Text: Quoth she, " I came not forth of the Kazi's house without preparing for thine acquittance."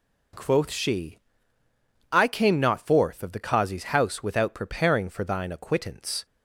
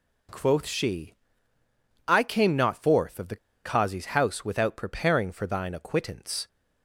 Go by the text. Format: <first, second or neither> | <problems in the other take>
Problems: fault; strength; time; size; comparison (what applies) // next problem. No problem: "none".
first | pauses between "the" and "Kazi's"; slight; at 3.3 s; 0.28 s long